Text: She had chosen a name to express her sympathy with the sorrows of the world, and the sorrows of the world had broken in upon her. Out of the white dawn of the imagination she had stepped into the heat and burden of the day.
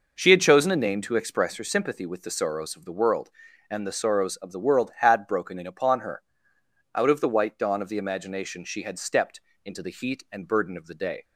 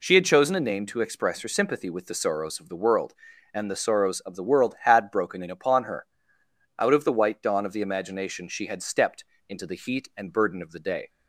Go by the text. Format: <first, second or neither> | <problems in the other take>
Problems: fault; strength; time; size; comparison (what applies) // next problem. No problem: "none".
second | starts louder than the rest; noticeable; until 1.6 s; 5.5 dB // pauses between "stepped" and "into"; slight; at 9.4 s; 0.24 s long; slight in the second